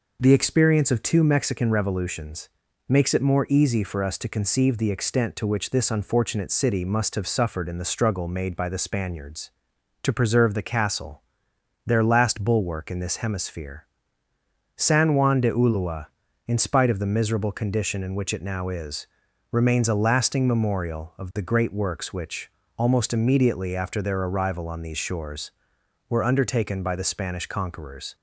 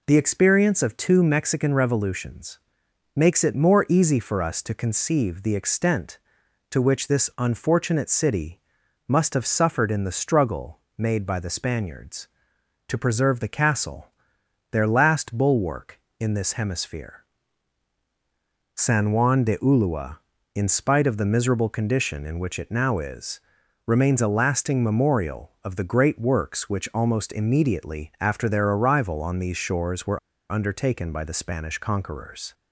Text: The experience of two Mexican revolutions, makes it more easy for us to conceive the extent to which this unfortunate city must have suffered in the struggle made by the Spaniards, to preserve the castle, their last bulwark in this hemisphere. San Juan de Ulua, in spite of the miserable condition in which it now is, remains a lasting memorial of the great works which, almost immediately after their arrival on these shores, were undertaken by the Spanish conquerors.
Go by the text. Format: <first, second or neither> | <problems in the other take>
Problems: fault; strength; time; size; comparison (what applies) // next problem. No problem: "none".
first | pauses between "city" and "must"; noticeable; at 8.5 s; 0.48 s long // pauses between "struggle" and "made"; slight; at 10.7 s; 0.18 s long // pauses between "were" and "undertaken"; slight; at 30.1 s; 0.32 s long